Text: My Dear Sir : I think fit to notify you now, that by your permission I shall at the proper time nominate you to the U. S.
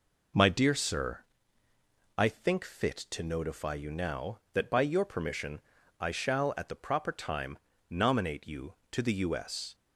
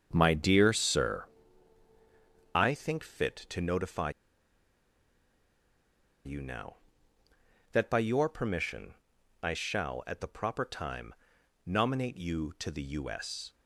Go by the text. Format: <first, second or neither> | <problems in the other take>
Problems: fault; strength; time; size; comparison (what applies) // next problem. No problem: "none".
first | starts louder than the rest; strong; until 1.1 s; 7.5 dB // pauses between "notify" and "you"; strong; at 4.0 s; 2.1 s long // pauses between "permission" and "I"; noticeable; at 8.9 s; 0.48 s long; also in the first // pauses between "time" and "nominate"; noticeable; at 11.1 s; 0.54 s long; slight in the first